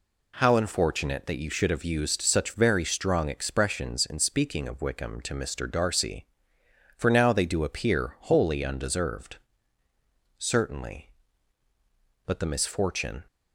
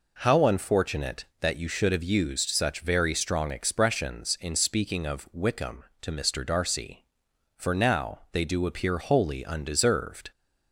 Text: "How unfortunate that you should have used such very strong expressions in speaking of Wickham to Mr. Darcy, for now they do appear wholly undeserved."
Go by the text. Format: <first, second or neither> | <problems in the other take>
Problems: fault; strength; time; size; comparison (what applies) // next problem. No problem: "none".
second | goes on to say "Certainly But the misfortune"; strong; from 10.4 s on; 2.8 s long